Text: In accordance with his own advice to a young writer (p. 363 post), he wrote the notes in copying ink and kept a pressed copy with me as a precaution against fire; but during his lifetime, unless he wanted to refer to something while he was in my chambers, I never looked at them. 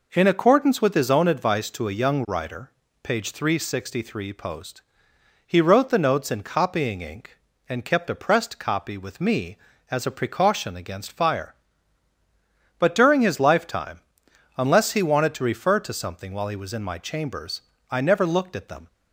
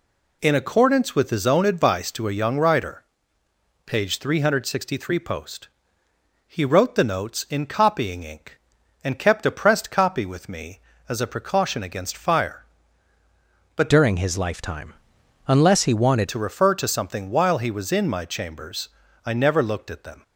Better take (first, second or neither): first